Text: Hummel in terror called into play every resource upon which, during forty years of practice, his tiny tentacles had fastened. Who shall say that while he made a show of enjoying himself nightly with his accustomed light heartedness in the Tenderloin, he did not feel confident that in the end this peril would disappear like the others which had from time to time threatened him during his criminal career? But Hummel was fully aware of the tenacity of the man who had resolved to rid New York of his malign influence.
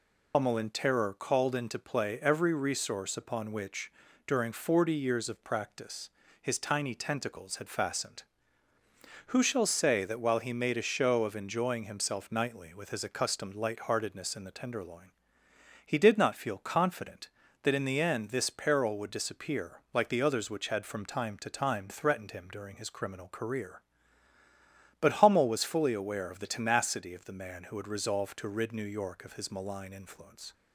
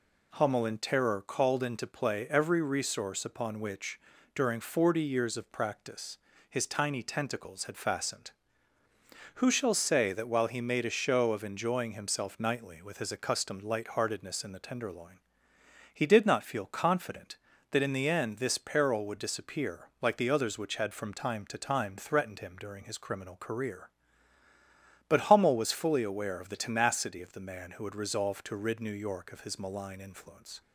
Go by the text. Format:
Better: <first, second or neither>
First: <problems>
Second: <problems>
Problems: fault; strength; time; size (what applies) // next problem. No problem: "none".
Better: second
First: loses the start of "Hummel"; at 0.3 s; 100 ms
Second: none